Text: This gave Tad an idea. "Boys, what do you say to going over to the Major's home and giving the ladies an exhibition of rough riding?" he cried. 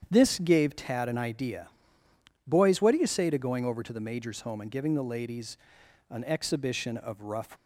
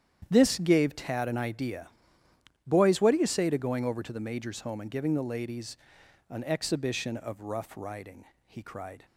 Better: second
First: starts louder than the rest; strong; until 1.1 s; 8.5 dB // pauses between "ladies" and "an"; noticeable; at 5.5 s; 0.52 s long // stops before "riding he cried"; at 7.5 s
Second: starts louder than the rest; strong; until 1.3 s; 9.5 dB // pauses between "ladies" and "an"; noticeable; at 5.7 s; 0.52 s long

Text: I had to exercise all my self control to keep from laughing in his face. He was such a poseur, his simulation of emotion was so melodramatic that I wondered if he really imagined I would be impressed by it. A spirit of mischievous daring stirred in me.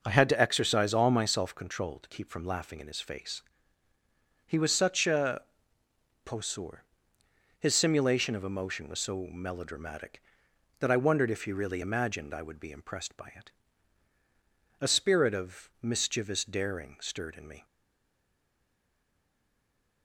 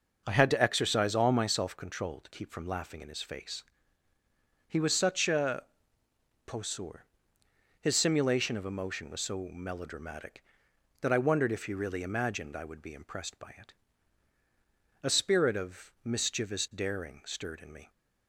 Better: second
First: pauses between "a" and "poseur"; noticeable; at 5.4 s; 0.82 s long // stays silent after the last word; from 17.6 s on; 2.4 s long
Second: pauses between "a" and "poseur"; noticeable; at 5.6 s; 0.82 s long

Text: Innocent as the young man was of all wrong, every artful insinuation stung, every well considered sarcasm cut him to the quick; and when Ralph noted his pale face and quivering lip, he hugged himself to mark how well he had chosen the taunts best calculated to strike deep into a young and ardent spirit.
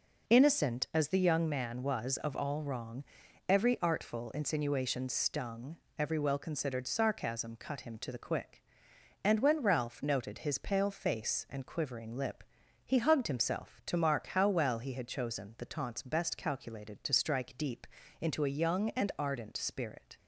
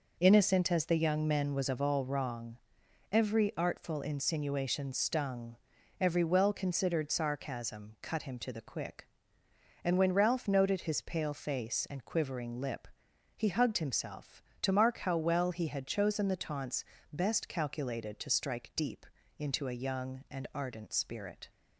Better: first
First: pauses between "deep" and "into"; slight; at 17.8 s; 0.34 s long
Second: says "men" for "man"; at 1.2 s // pauses between "taunts" and "best"; slight; at 16.8 s; 0.26 s long // pauses between "deep" and "into"; slight; at 19.0 s; 0.32 s long

